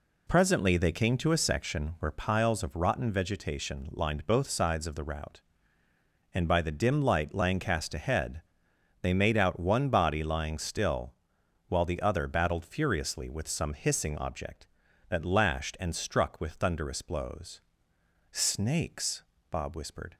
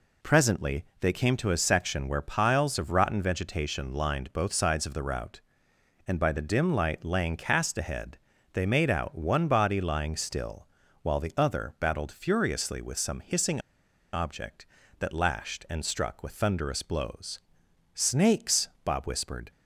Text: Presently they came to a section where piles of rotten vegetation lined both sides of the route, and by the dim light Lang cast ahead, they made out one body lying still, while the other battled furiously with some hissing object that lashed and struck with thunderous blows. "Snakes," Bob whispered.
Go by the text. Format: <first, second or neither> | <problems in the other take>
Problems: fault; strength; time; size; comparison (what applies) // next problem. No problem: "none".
first | pauses between "Presently" and "they"; slight; at 0.8 s; 0.16 s long // pauses between "hissing" and "object"; noticeable; at 13.6 s; 0.52 s long